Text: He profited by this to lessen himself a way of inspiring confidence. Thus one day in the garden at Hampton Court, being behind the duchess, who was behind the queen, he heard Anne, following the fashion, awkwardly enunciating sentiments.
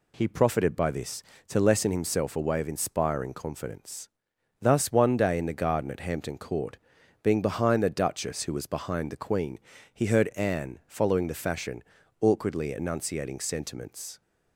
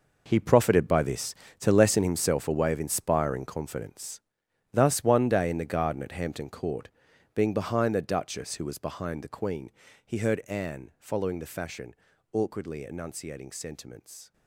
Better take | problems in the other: first | gets quieter; strong; throughout; 13.5 dB

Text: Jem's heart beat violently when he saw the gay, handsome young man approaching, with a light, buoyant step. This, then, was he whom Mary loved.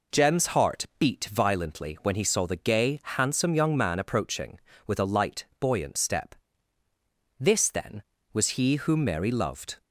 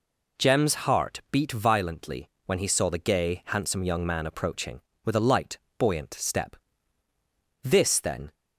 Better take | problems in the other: first | pauses between "violently" and "when"; slight; at 2.2 s; 0.18 s long // stops before "was he whom Mary loved"; at 8.3 s

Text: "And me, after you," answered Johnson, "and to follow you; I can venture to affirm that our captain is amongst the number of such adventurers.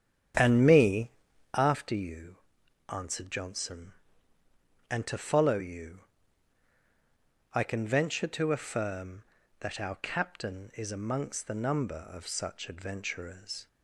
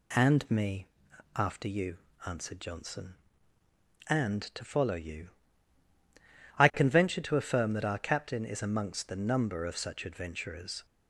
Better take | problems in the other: second | starts louder than the rest; strong; until 1.7 s; 8.5 dB

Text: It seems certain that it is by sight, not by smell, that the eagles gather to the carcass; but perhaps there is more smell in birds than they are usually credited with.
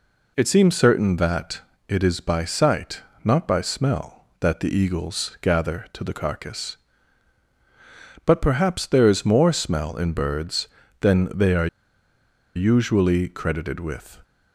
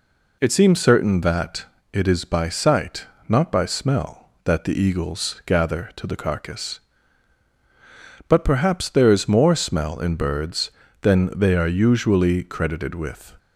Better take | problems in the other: second | pauses between "that" and "it"; slight; at 1.6 s; 0.26 s long; slight in the second // pauses between "are" and "usually"; noticeable; at 11.6 s; 0.87 s long

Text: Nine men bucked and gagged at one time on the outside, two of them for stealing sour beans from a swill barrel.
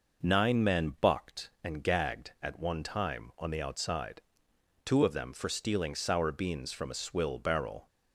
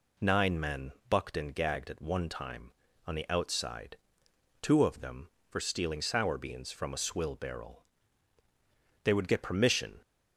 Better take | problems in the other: first | pauses between "men" and "bucked"; slight; at 0.9 s; 0.18 s long // goes on to say "They would get permission"; noticeable; from 9.0 s on; 0.98 s long

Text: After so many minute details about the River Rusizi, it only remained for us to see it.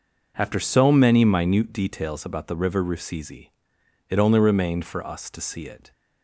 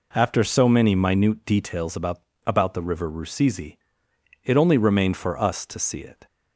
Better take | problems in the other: first | says "about" twice; at 2.4 s

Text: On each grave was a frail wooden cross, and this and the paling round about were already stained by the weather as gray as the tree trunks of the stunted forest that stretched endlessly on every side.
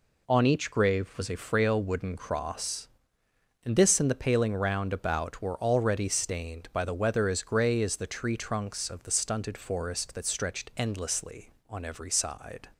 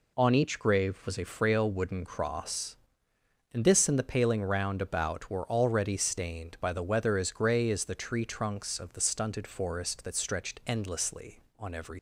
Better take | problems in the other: first | stops before "side"; at 11.9 s

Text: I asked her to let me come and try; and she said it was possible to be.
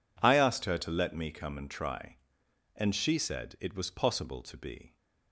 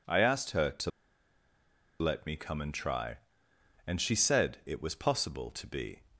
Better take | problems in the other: first | pauses between "to" and "let"; at 0.8 s; 1.1 s long

